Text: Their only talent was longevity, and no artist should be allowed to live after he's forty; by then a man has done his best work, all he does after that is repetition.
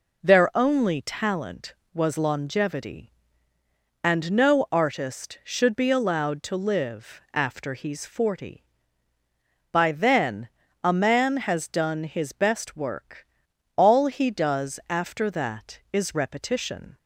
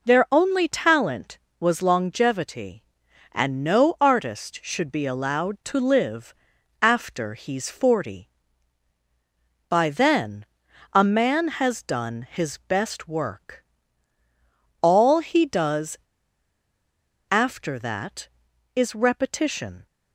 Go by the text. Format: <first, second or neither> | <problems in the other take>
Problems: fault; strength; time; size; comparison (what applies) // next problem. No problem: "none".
first | pauses between "live" and "after"; noticeable; at 6.3 s; 0.48 s long // pauses between "then" and "a"; noticeable; at 10.4 s; 0.46 s long; slight in the first // pauses between "does" and "after"; strong; at 15.9 s; 1.3 s long